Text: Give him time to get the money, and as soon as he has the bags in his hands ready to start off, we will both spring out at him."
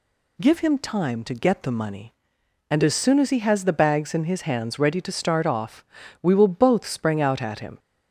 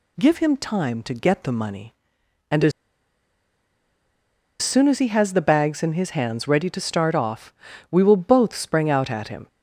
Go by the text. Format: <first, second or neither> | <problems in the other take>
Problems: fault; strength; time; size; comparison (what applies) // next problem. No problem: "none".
first | pauses between "as" and "soon"; strong; at 2.7 s; 1.8 s long